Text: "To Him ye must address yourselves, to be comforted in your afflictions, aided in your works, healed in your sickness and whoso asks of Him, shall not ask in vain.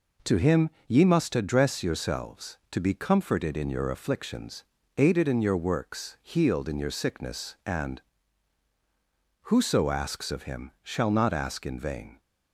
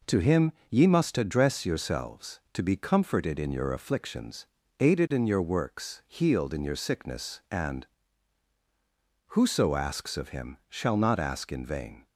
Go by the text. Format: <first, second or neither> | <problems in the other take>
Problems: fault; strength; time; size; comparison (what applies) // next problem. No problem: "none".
neither | pauses between "Him" and "ye"; slight; the same in both // pauses between "and" and "whoso"; strong; the same in both